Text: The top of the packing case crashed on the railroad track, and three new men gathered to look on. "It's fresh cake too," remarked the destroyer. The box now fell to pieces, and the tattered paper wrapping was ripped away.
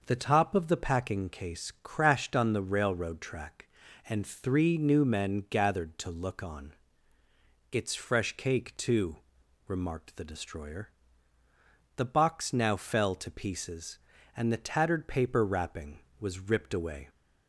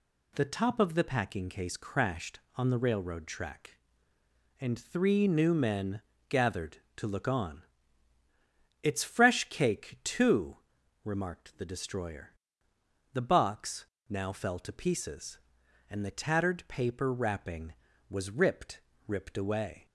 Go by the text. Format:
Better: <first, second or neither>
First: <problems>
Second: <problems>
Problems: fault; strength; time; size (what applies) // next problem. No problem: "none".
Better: first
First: none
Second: pauses between "men" and "gathered"; slight; at 6.0 s; 0.28 s long // pauses between "box" and "now"; slight; at 13.8 s; 0.24 s long // says "ripped" twice; at 19.0 s